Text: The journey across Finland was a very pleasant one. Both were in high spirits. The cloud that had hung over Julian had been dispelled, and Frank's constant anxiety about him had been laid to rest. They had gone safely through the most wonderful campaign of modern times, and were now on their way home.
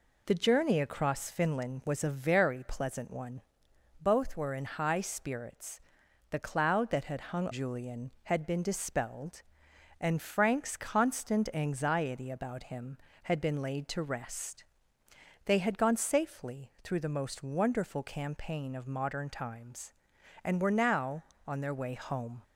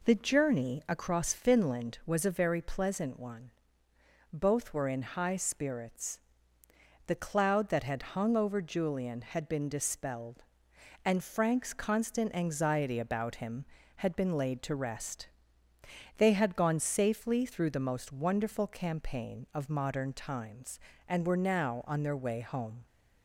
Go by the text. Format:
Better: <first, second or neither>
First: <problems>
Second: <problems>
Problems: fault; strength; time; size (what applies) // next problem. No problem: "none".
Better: second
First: skips "over"; at 7.5 s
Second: none